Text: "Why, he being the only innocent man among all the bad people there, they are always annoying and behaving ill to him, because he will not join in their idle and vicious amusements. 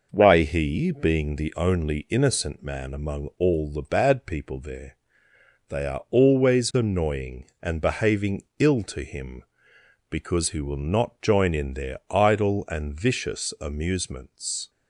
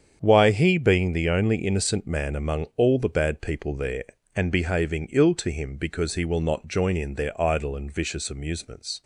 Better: first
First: none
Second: starts louder than the rest; strong; until 1.2 s; 8 dB // skips "they are always annoying"; at 4.1 s

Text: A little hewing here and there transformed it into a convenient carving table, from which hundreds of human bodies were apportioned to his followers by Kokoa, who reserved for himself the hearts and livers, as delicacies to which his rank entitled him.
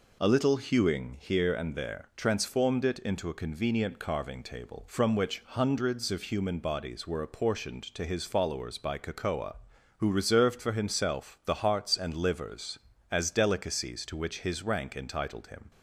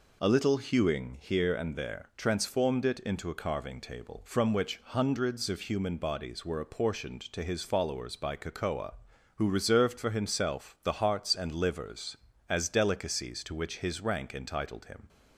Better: first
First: none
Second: skips "convenient"; at 3.3 s

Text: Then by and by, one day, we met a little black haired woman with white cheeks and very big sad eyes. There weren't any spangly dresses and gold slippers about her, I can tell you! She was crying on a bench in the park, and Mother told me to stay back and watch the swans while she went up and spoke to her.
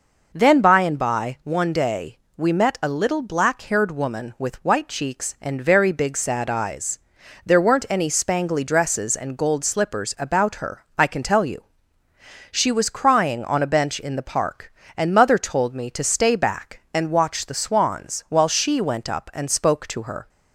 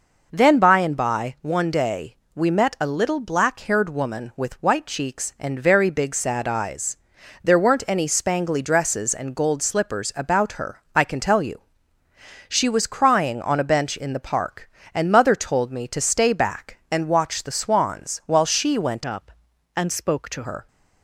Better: first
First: none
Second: changes voice from "up" to "to"; from 19.0 to 20.4 s; 1.4 s long

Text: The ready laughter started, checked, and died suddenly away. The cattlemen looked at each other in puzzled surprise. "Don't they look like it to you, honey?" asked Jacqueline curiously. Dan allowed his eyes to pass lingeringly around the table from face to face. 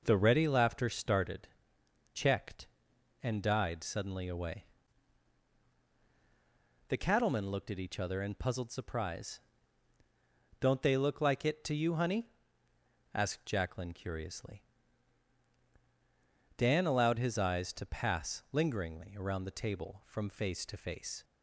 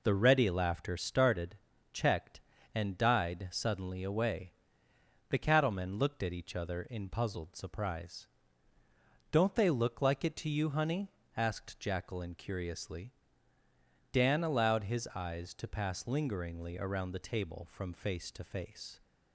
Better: neither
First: none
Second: none

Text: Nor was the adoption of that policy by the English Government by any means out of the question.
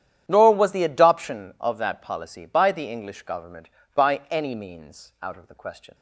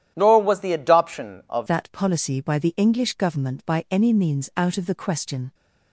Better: first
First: starts louder than the rest; strong; until 1.2 s; 10 dB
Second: starts louder than the rest; strong; until 1.1 s; 11 dB // changes voice at "that"; from 1.6 s on; 3.9 s long

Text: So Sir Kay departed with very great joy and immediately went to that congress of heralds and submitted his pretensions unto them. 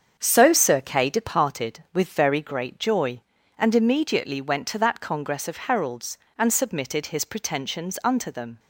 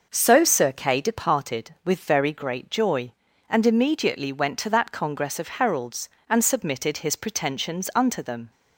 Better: second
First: gets quieter; throughout; 6.5 dB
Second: none

